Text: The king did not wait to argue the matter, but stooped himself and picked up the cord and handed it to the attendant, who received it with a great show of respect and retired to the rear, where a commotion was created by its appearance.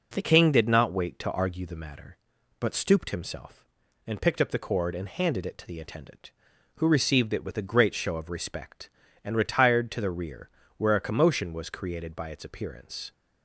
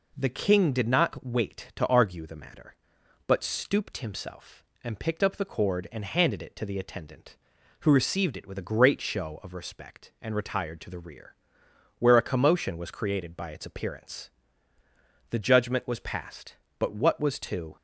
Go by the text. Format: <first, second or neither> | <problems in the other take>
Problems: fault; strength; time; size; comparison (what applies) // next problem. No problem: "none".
first | goes on to say "The judgment was passed but what was to"; strong; from 15.3 s on; 2.4 s long